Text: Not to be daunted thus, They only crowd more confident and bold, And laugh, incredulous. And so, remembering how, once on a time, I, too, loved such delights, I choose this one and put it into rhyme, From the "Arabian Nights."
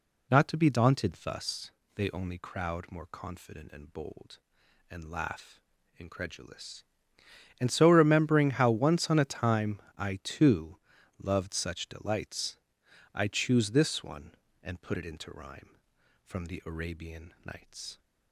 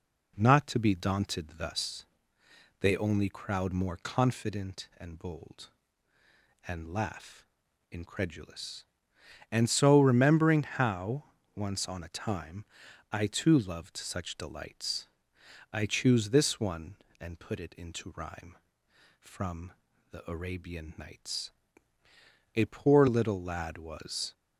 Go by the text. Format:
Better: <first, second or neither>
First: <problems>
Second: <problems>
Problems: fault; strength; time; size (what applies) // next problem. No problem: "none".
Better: first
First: none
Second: pauses between "From" and "the"; at 19.7 s; 0.38 s long // goes on to say "A poor little lad was"; strong; from 22.5 s on; 1.7 s long